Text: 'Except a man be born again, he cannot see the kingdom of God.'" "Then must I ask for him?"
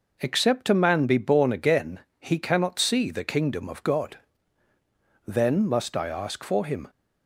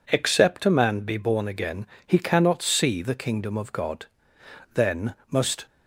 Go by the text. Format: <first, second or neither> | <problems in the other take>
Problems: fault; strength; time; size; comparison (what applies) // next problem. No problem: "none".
first | pauses between "Then" and "must"; slight; at 5.1 s; 0.16 s long // stops before "I ask for him"; at 5.6 s